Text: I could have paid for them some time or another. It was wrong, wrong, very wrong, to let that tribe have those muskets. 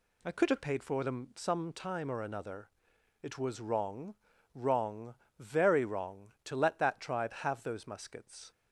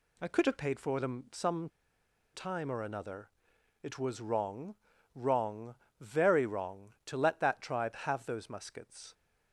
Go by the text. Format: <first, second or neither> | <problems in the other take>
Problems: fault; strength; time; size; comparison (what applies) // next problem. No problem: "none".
first | pauses between "some" and "time"; noticeable; at 1.6 s; 0.65 s long